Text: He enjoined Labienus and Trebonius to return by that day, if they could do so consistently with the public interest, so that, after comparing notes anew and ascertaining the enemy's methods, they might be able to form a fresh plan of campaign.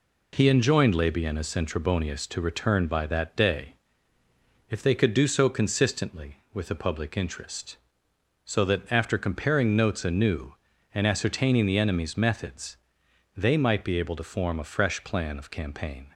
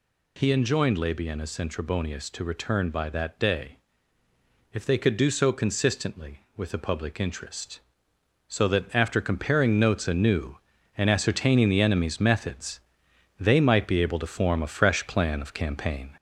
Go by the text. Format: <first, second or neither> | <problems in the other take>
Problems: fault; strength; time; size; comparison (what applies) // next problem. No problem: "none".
first | gets louder; slight; throughout; 3.5 dB